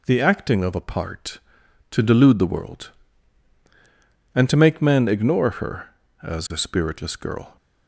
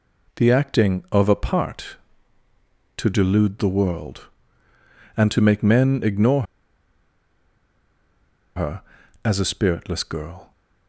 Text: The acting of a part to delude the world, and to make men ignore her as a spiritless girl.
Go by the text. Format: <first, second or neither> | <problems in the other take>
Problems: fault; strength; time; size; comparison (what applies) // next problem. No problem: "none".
first | pauses between "ignore" and "her"; strong; at 6.4 s; 2.1 s long